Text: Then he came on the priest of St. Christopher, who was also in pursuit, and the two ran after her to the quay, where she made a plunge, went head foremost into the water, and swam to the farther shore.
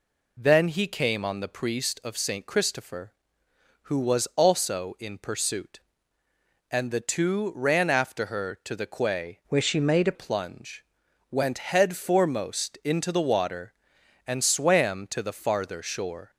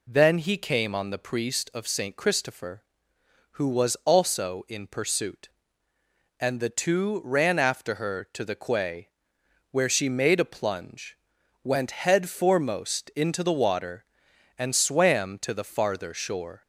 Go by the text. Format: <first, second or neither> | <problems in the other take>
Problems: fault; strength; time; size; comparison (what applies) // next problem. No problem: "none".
second | changes voice from "where" to "a"; from 9.4 to 10.1 s; 0.7 s long